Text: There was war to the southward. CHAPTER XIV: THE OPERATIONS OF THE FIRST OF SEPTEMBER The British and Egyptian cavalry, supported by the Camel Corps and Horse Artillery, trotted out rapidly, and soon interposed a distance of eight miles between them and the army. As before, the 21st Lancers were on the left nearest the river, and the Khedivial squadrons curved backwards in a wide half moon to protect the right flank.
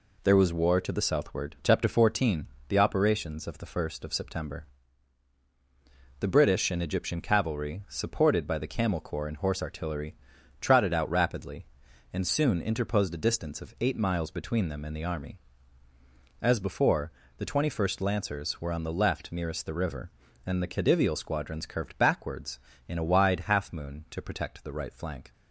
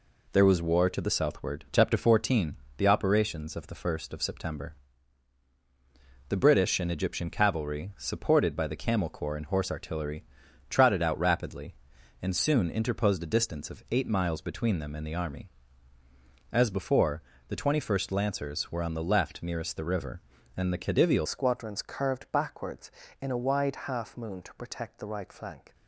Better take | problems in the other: first | pauses between "SEPTEMBER" and "The"; strong; at 4.7 s; 1.5 s long; strong in the first // changes voice at "squadrons"; from 21.2 s on; 4.5 s long

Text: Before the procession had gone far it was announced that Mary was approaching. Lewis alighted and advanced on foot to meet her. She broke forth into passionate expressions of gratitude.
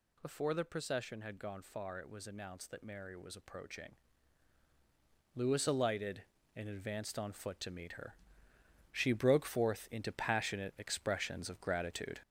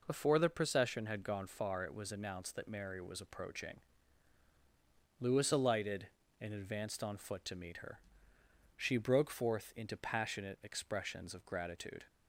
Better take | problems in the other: second | gets louder; noticeable; throughout; 5.5 dB

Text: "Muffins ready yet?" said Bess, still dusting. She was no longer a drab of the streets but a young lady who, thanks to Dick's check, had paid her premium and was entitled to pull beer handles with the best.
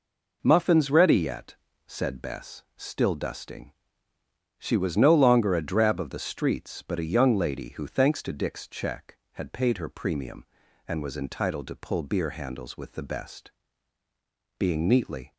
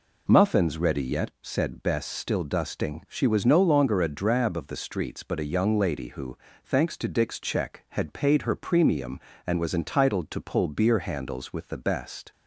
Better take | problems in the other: second | goes on to say "Being neatly"; noticeable; from 14.5 s on; 0.74 s long

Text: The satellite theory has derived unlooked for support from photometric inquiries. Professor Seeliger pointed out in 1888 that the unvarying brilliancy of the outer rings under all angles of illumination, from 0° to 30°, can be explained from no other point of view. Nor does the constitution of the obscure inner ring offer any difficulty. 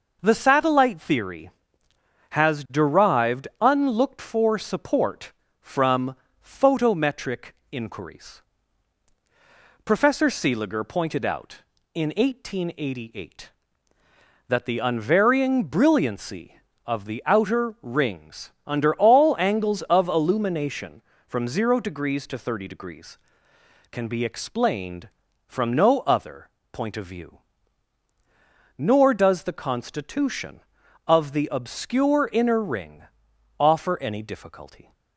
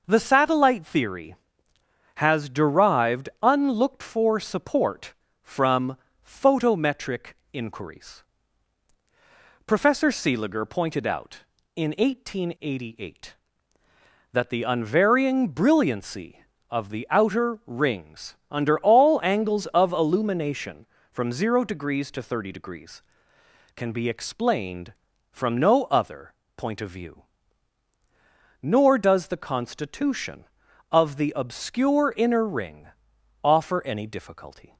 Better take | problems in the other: neither | pauses between "from" and "photometric"; slight; the same in both // pauses between "photometric" and "inquiries"; slight; the same in both // pauses between "other" and "point"; slight; the same in both // pauses between "ring" and "offer"; noticeable; the same in both

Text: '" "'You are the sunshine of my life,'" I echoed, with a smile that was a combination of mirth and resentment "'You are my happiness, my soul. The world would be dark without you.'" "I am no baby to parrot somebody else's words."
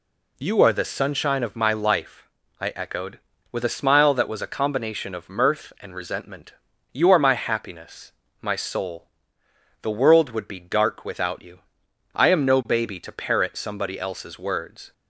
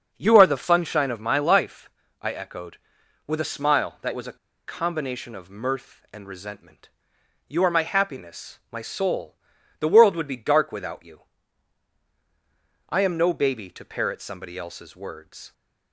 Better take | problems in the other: first | starts louder than the rest; until 1.1 s; 6.5 dB // pauses between "a" and "combination"; slight; at 4.3 s; 0.30 s long // pauses between "resentment" and "You"; noticeable; at 6.8 s; 0.58 s long; also in the first

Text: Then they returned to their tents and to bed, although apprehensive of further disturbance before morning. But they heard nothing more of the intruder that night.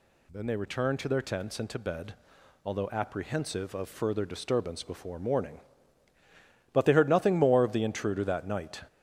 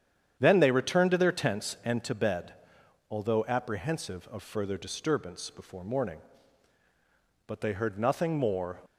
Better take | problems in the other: first | starts louder than the rest; strong; until 1.4 s; 9 dB // stops before "of the intruder that night"; at 8.8 s

